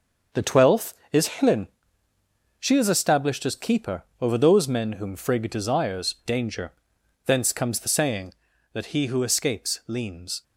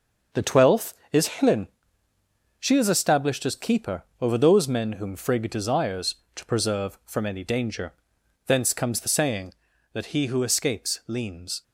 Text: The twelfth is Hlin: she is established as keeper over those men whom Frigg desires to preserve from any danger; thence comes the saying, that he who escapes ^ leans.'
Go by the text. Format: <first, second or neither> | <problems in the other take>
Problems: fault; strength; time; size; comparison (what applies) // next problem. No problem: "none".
second | starts louder than the rest; until 1.5 s; 6.5 dB; also in the second // pauses between "keeper" and "over"; slight; at 4.0 s; 0.18 s long; slight in the second // skips "to preserve from any"; at 6.2 s